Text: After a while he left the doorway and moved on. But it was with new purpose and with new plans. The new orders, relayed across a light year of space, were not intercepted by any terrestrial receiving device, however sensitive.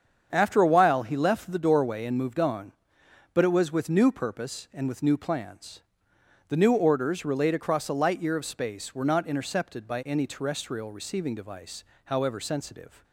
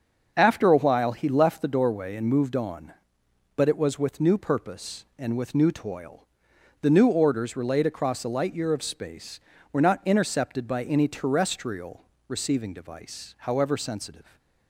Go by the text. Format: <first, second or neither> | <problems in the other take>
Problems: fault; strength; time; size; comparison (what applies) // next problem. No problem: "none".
first | starts louder than the rest; until 1.3 s; 6.5 dB; strong in the first // says "toil" for "plans"; at 5.6 s // pauses between "terrestrial" and "receiving"; slight; at 12.0 s; 0.24 s long